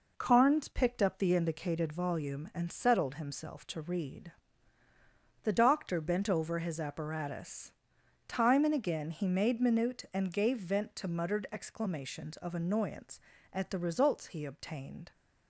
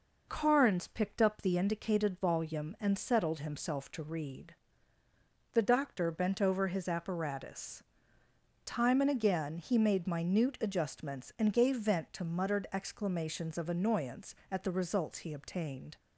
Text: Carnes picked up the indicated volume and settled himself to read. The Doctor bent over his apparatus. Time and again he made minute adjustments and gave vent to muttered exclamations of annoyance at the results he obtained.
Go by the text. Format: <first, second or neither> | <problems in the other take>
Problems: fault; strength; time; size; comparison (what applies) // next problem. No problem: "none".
second | skips "adjustments"; at 10.0 s